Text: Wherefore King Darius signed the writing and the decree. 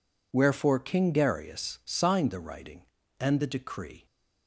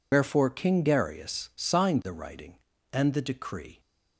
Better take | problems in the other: first | loses the start of "Wherefore"; at 0.1 s; 85 ms

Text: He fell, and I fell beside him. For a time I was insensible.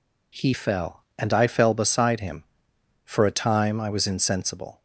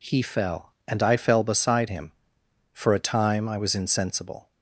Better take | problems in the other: neither | none

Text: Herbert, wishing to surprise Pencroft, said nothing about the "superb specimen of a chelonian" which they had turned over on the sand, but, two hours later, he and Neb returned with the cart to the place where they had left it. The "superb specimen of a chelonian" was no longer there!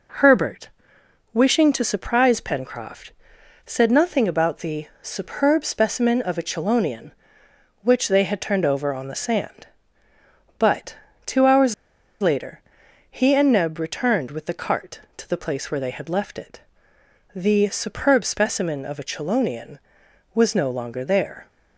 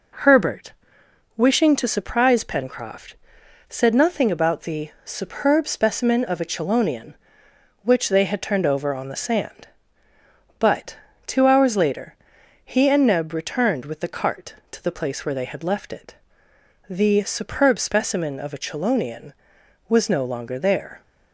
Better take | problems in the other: second | pauses between "hours" and "later"; noticeable; at 11.7 s; 0.48 s long

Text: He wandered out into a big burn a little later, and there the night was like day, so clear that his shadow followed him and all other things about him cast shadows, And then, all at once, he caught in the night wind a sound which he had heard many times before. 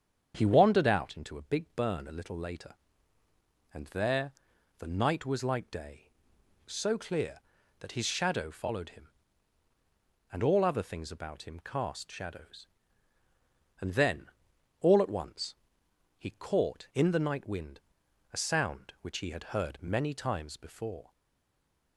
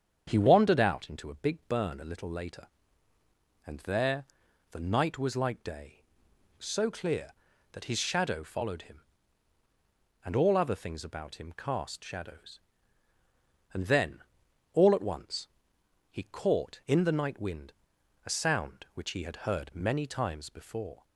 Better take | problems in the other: second | starts louder than the rest; strong; until 1.3 s; 7.5 dB; strong in the second // pauses between "there" and "the"; noticeable; at 4.3 s; 0.46 s long; noticeable in the second // pauses between "wind" and "a"; noticeable; at 17.7 s; 0.54 s long; noticeable in the second // stays silent after the last word; slight; from 21.1 s on; 0.8 s long

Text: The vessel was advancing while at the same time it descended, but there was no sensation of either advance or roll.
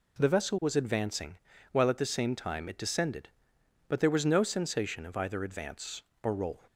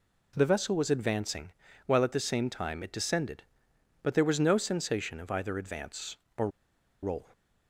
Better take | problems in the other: first | pauses between "advancing" and "while"; slight; at 1.5 s; 0.34 s long; slight in the first // pauses between "or" and "roll"; noticeable; at 6.4 s; 0.54 s long

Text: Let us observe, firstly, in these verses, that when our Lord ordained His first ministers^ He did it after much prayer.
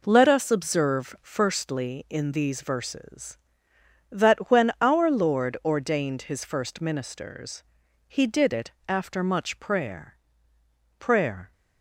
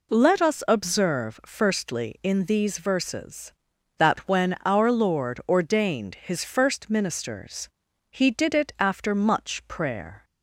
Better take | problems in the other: second | pauses between "ministers" and "He"; at 7.6 s; 0.42 s long; also in the second // pauses between "it" and "after"; slight; at 8.7 s; 0.16 s long // says "prayer" twice; at 10.9 s

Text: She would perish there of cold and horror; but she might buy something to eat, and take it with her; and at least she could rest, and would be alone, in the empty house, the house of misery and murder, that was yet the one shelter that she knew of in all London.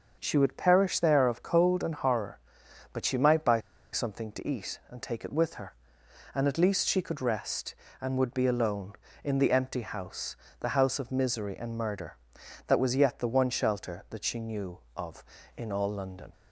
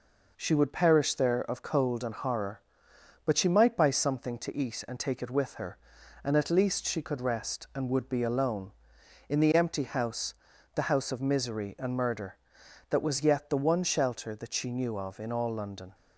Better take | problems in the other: second | starts louder than the rest; until 1.2 s; 6.5 dB // pauses between "buy" and "something"; slight; at 3.6 s; 0.32 s long

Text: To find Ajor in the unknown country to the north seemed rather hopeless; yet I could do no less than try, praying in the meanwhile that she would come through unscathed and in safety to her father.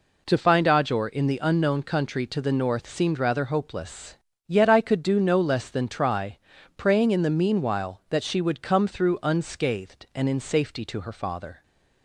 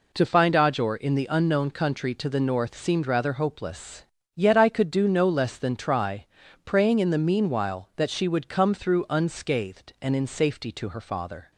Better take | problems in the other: neither | none

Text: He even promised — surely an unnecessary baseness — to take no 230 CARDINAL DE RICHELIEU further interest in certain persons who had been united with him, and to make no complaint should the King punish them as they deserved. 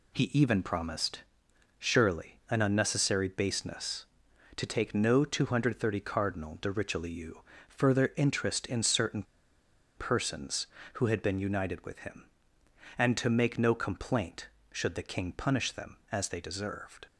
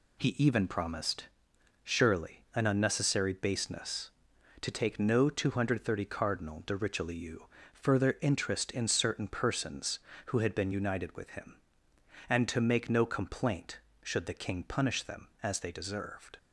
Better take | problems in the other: second | pauses between "RICHELIEU" and "further"; slight; at 7.4 s; 0.26 s long; slight in the second // pauses between "certain" and "persons"; noticeable; at 9.2 s; 0.74 s long

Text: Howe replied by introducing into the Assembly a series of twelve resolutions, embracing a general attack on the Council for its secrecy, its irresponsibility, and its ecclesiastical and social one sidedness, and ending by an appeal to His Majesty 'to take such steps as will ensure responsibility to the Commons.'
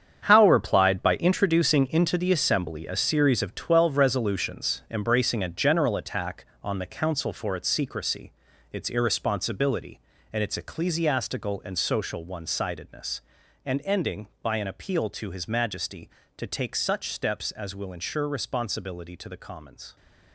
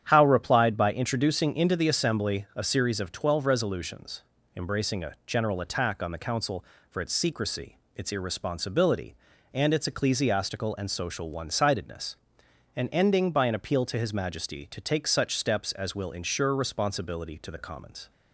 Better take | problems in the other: second | gets quieter; strong; throughout; 11.5 dB // starts louder than the rest; strong; until 1.2 s; 8 dB; strong in the second

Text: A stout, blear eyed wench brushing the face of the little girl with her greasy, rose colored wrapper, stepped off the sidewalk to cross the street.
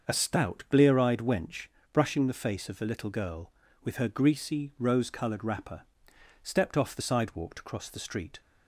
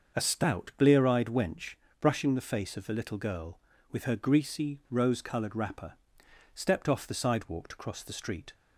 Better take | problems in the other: neither | starts louder than the rest; the same in both // pauses between "wench" and "brushing"; slight; the same in both

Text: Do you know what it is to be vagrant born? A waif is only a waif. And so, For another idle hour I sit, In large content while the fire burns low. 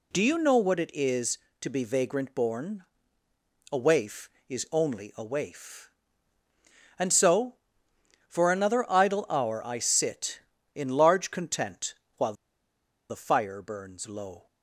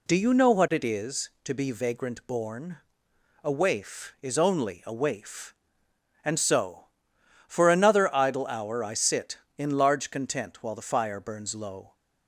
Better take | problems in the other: second | pauses between "content" and "while"; slight; at 11.9 s; 0.24 s long // pauses between "while" and "the"; noticeable; at 12.3 s; 0.75 s long

